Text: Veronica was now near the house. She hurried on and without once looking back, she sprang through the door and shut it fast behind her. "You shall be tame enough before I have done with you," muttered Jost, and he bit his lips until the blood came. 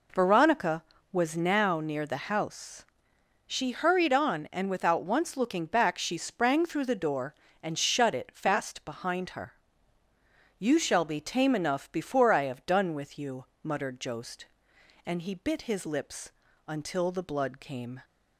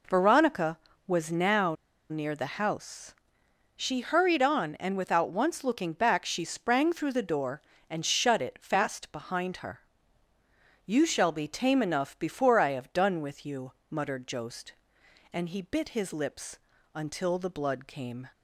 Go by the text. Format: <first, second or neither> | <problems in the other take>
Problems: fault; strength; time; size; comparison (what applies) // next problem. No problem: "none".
first | pauses between "now" and "near"; at 1.7 s; 0.36 s long // pauses between "lips" and "until"; slight; at 16.5 s; 0.36 s long; slight in the first